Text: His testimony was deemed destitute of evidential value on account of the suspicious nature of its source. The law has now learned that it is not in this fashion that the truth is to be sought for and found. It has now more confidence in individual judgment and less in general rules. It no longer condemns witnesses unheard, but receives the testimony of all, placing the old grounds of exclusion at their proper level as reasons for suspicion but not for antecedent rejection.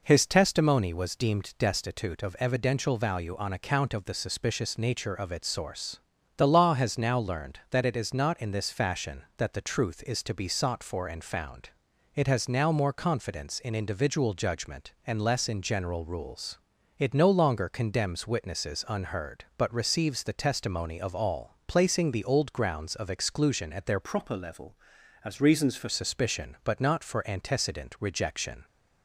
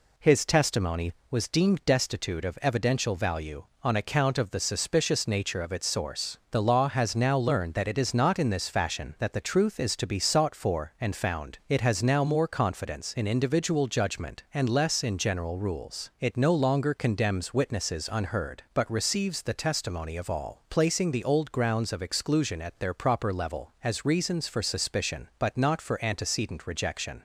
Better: second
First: changes voice from "proper" to "for"; from 24.0 to 25.8 s; 1.8 s long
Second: none

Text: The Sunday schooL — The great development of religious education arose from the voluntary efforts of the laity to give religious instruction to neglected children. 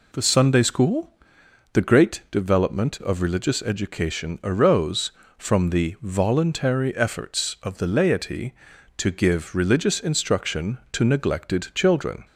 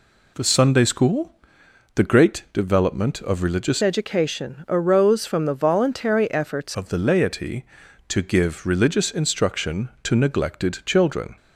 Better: first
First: none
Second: changes voice from "education" to "efforts"; from 3.8 to 6.7 s; 2.9 s long

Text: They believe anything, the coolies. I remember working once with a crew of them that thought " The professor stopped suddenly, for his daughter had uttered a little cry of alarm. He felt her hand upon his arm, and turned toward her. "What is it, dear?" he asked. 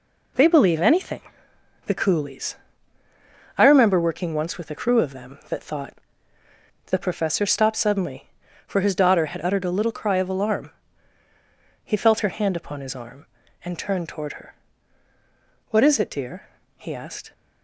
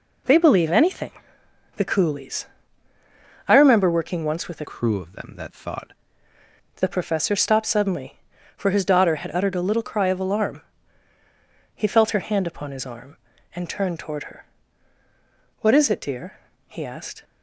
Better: first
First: none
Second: changes voice from "crew" to "thought"; from 4.6 to 5.9 s; 1.3 s long

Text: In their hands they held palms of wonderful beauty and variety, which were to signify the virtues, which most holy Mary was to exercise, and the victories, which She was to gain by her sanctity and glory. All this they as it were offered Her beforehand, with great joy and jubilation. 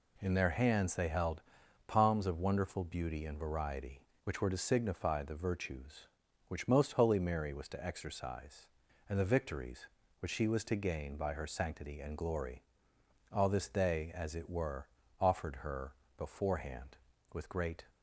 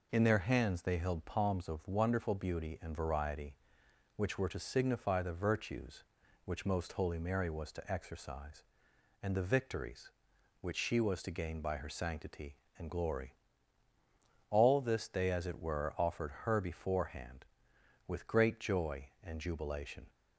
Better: second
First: pauses between "held" and "palms"; at 1.4 s; 0.44 s long // pauses between "were" and "offered"; slight; at 14.8 s; 0.34 s long // pauses between "Her" and "beforehand"; slight; at 15.9 s; 0.24 s long // stops before "joy and jubilation"; at 17.8 s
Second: none

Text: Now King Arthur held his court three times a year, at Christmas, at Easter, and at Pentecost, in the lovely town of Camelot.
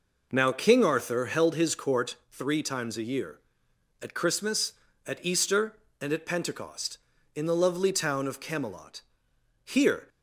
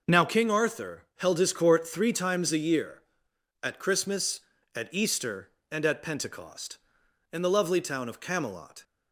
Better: second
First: goes on to say "Here"; slight; from 9.6 s on; 0.44 s long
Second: none

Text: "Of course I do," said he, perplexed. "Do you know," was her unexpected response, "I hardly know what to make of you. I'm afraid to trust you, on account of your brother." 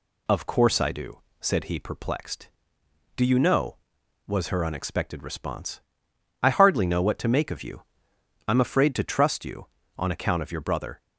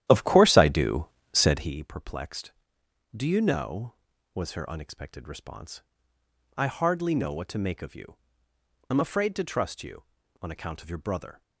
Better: first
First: none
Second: starts louder than the rest; strong; until 1.8 s; 12 dB

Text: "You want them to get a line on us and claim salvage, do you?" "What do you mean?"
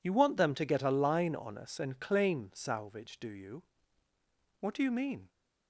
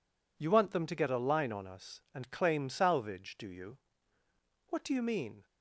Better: neither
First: none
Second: none

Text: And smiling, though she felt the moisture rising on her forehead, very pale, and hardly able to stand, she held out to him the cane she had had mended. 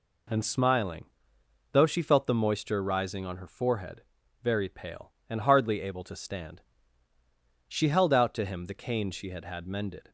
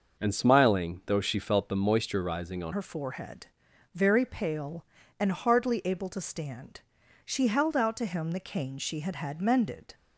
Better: first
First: none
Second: changes voice at "her"; from 2.7 s on; 7.2 s long

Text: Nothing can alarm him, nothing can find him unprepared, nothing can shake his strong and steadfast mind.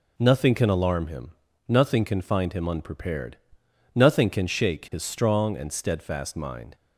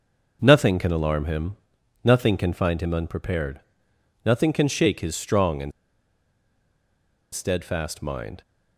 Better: first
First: none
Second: pauses between "and" and "steadfast"; strong; at 5.7 s; 1.6 s long

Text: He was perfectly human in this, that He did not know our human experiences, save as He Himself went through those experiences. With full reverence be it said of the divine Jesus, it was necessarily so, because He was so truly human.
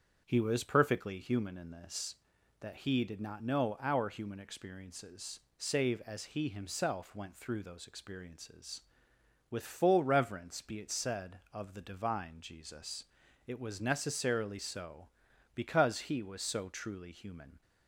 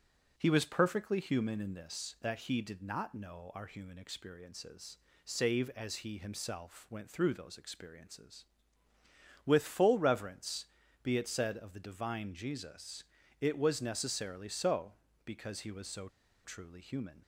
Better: first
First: starts louder than the rest; strong; until 1.2 s; 7.5 dB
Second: starts louder than the rest; until 1.3 s; 6.5 dB // pauses between "reverence" and "be"; slight; at 10.6 s; 0.36 s long // pauses between "so" and "truly"; at 16.0 s; 0.37 s long

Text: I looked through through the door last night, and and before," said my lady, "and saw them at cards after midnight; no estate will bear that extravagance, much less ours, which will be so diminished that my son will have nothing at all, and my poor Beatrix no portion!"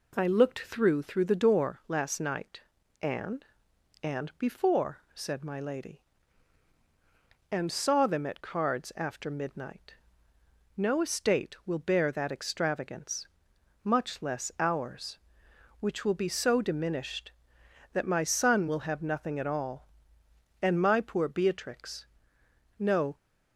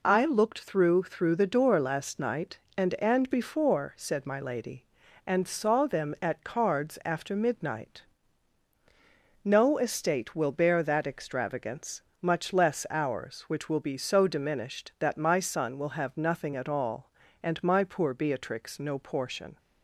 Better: second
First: pauses between "Beatrix" and "no"; noticeable; at 22.0 s; 0.74 s long // stops before "portion"; at 23.1 s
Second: none

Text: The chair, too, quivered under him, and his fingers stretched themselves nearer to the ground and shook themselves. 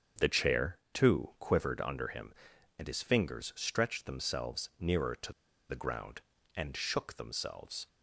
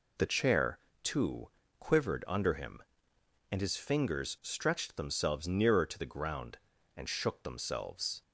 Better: second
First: starts louder than the rest; strong; until 1.3 s; 7 dB // pauses between "to" and "the"; at 5.3 s; 0.38 s long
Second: none

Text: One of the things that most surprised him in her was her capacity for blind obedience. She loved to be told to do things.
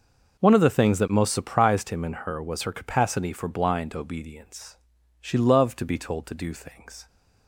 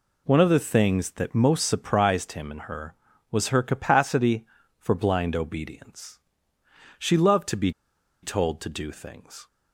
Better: first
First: none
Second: pauses between "be" and "told"; noticeable; at 7.7 s; 0.51 s long

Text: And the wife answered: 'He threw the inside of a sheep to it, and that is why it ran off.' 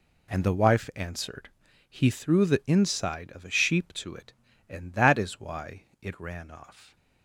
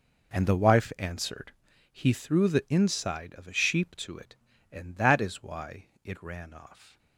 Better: first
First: pauses between "why" and "it"; slight; at 5.8 s; 0.18 s long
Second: starts louder than the rest; noticeable; until 1.6 s; 4.5 dB // pauses between "why" and "it"; slight; at 5.8 s; 0.18 s long

